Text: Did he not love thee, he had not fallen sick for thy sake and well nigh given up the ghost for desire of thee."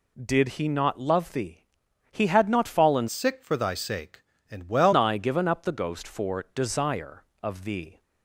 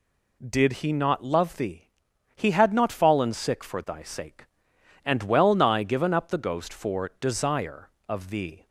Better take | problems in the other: second | changes voice from "sick" to "well"; from 3.0 to 4.9 s; 1.9 s long

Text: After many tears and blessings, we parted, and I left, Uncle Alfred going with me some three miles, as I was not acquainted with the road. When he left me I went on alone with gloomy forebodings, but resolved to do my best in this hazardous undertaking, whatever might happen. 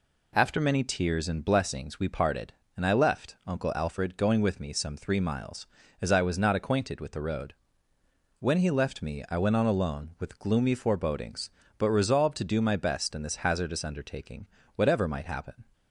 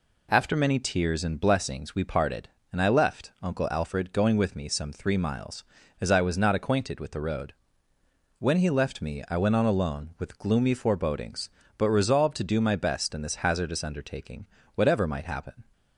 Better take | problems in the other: neither | none

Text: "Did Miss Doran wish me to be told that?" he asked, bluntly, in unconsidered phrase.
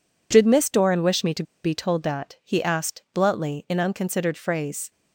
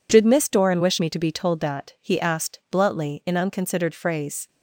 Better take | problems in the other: second | pauses between "to" and "be"; slight; at 1.4 s; 0.20 s long

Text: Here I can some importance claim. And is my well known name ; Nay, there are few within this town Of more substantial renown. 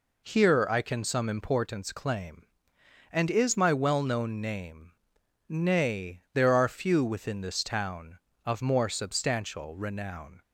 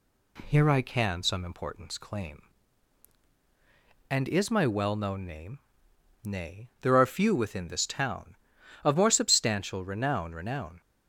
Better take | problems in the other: first | says "renown" twice; at 10.3 s

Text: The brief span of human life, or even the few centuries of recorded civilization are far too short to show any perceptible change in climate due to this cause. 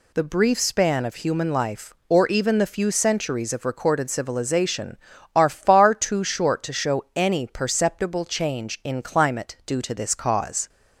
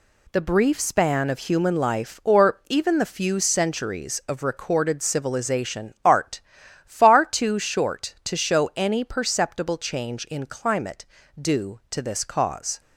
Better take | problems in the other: first | says "art" for "are"; at 6.0 s // pauses between "climate" and "due"; slight; at 11.0 s; 0.36 s long

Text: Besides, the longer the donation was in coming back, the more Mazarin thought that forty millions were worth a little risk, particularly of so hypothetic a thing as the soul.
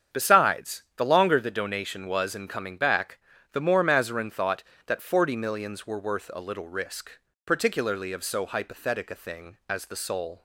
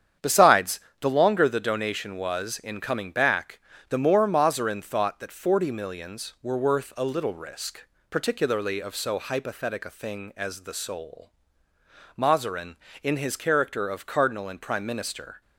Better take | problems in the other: first | starts louder than the rest; strong; until 1.4 s; 8.5 dB; strong in the first // goes on to say "Mazarin in his character of cardinal and prime minister"; strong; from 12.1 s on; 3.2 s long

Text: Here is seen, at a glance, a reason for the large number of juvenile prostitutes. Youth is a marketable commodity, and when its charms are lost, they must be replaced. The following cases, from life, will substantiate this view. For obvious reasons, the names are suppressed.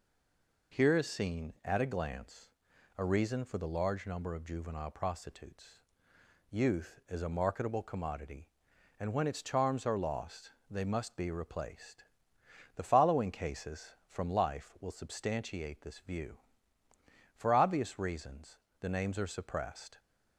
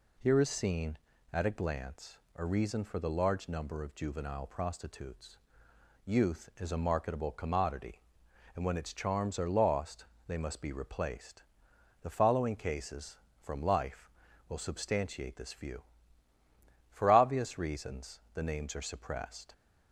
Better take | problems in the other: second | stays silent before the first word; slight; until 0.7 s; 0.7 s long

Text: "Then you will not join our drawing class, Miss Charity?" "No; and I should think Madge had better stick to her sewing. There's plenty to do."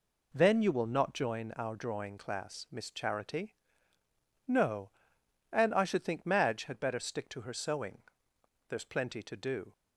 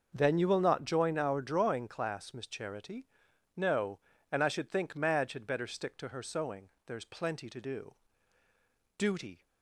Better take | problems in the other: first | goes on to say "Duty"; slight; from 8.9 s on; 0.48 s long

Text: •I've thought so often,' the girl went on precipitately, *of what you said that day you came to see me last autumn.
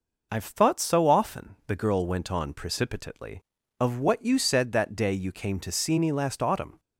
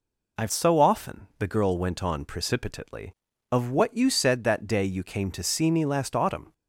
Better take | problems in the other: first | skips "thought"; at 0.5 s

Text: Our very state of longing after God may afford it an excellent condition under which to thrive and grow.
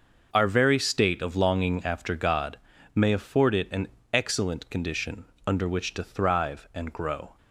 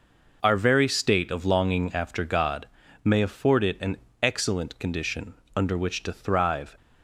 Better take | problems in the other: first | pauses between "God" and "may"; slight; at 2.6 s; 0.36 s long; slight in the first // pauses between "an" and "excellent"; slight; at 3.9 s; 0.26 s long; slight in the first // pauses between "condition" and "under"; slight; at 5.3 s; 0.24 s long; slight in the first // stops before "and grow"; at 6.7 s

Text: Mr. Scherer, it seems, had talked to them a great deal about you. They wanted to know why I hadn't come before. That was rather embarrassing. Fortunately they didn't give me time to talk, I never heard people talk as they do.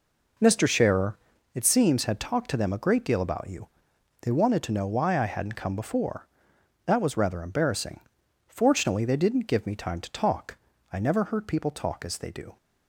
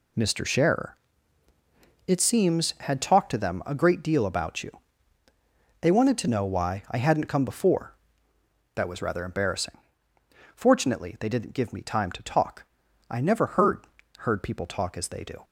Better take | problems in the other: first | says "heard" twice; at 14.1 s

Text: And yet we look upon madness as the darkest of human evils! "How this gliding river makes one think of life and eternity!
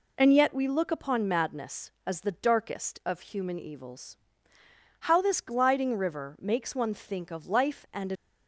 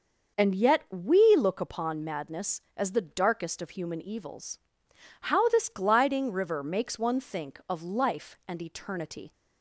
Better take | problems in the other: second | stops before "eternity"; at 8.1 s

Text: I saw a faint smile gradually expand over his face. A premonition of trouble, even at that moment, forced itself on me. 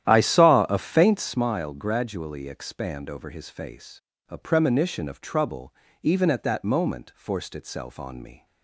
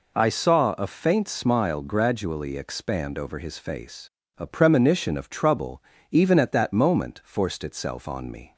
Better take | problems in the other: second | starts louder than the rest; strong; until 1.4 s; 11.5 dB

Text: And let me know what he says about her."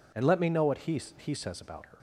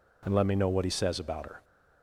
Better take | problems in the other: second | says "he" twice; at 1.1 s

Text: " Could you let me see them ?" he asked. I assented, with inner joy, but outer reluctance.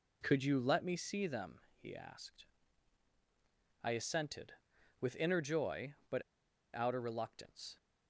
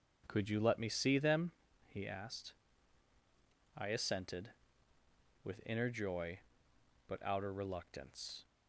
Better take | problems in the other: second | pauses between "but" and "outer"; noticeable; at 6.2 s; 0.51 s long

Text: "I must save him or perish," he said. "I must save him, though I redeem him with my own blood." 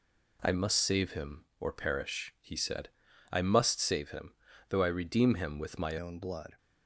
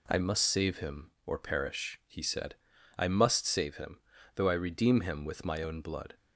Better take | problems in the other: second | changes voice at "own"; from 5.9 s on; 0.6 s long

